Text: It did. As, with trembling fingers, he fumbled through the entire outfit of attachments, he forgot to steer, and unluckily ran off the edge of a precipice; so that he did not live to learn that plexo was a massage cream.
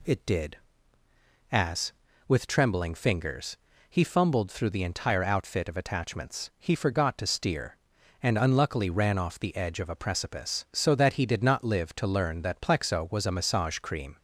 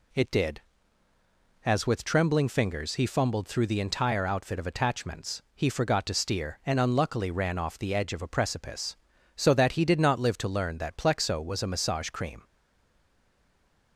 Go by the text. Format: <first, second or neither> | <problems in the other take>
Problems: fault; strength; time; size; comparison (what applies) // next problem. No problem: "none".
first | stays silent after the last word; noticeable; from 12.4 s on; 1.5 s long